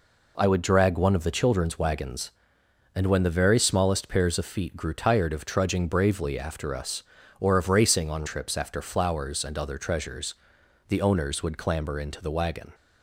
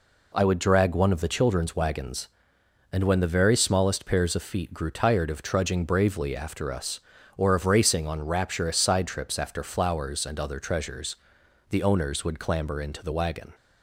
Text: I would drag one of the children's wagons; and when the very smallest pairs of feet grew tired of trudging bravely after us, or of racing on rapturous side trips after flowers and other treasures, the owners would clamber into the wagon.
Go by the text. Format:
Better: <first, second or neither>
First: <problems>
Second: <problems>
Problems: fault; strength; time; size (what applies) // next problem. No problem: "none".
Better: second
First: skips "rapturous side"; at 8.2 s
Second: none